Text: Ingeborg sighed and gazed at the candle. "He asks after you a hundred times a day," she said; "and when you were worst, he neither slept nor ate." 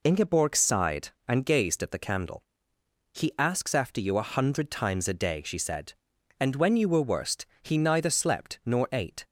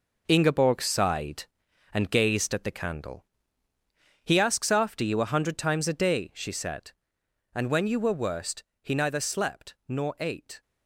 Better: first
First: none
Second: gets quieter; strong; throughout; 9 dB

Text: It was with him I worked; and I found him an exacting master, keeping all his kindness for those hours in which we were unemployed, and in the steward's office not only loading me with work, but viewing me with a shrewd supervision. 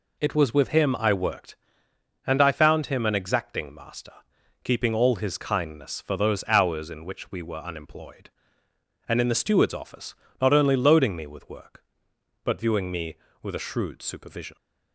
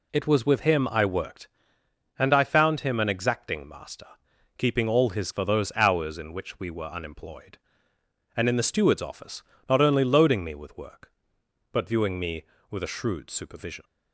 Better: first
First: pauses between "office" and "not"; slight; at 10.1 s; 0.26 s long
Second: skips "kindness"; at 5.3 s // pauses between "office" and "not"; slight; at 9.4 s; 0.26 s long

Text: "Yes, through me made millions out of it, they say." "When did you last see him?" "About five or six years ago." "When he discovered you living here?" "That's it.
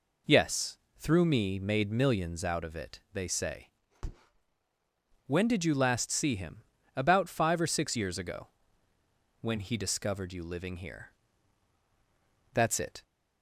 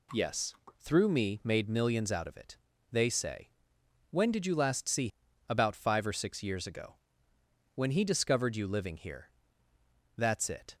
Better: first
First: none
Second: skips "him"; at 5.2 s

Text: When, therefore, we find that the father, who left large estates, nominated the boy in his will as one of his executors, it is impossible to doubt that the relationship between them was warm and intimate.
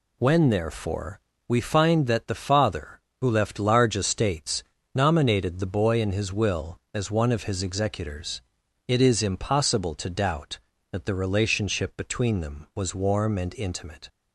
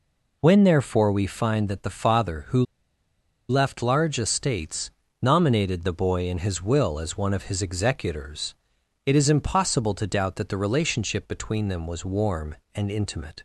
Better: first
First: none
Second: pauses between "who" and "left"; noticeable; at 2.6 s; 0.86 s long

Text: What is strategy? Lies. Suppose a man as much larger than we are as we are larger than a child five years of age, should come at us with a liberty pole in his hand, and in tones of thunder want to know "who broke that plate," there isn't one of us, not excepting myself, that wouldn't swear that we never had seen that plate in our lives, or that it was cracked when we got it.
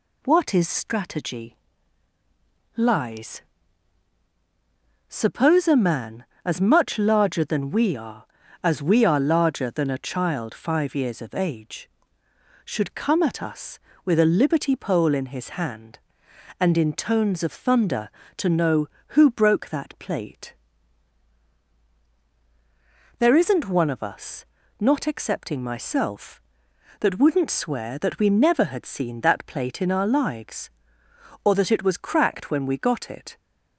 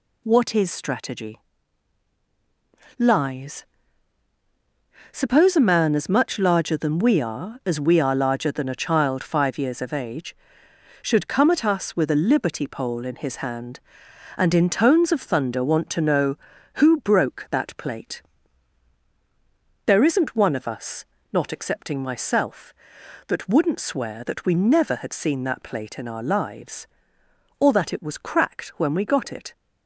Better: second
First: skips "want"; at 18.2 s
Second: none

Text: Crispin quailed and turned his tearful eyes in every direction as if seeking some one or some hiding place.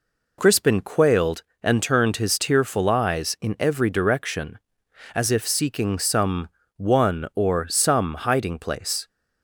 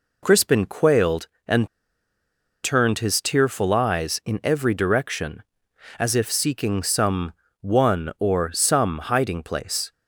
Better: first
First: pauses between "some" and "one"; slight; at 6.4 s; 0.26 s long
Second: pauses between "and" and "turned"; noticeable; at 1.6 s; 0.95 s long // pauses between "some" and "one"; slight; at 7.3 s; 0.26 s long

